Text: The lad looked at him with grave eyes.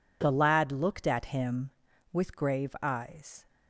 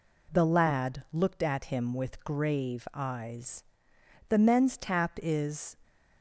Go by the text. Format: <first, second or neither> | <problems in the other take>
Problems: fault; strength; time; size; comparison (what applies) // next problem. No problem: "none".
first | goes on to say "The men's tap is"; from 4.2 s on; 1.4 s long